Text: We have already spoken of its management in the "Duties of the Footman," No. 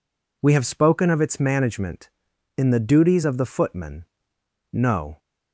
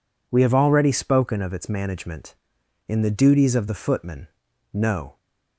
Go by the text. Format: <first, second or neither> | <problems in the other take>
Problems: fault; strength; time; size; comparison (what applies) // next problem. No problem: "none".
second | skips "already"; at 0.6 s